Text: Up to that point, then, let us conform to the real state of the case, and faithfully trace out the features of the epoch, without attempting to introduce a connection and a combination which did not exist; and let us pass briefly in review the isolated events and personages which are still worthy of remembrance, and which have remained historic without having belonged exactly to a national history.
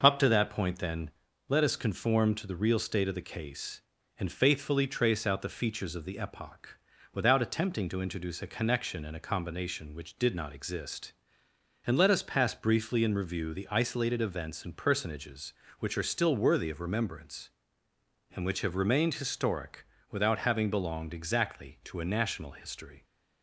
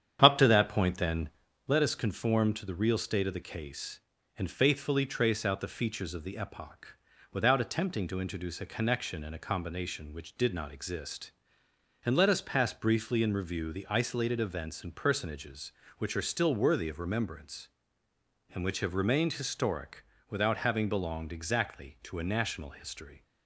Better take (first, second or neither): first